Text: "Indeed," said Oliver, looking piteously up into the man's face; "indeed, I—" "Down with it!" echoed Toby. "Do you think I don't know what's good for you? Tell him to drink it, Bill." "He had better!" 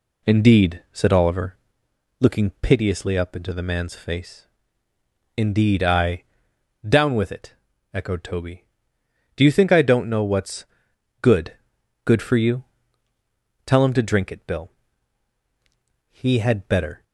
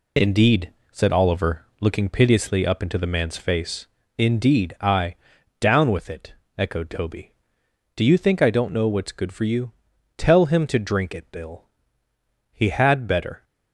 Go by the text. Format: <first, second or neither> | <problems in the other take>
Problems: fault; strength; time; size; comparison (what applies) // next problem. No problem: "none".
second | pauses between "what's" and "good"; noticeable; at 10.6 s; 0.56 s long // says "good" twice; at 12.0 s